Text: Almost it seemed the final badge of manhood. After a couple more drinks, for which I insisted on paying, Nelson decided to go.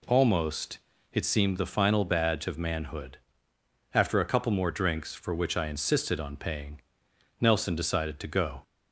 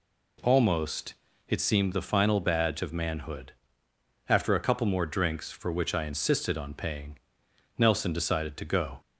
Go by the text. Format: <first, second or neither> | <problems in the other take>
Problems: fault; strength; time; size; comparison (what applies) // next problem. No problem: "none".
neither | pauses between "Almost" and "it"; slight; the same in both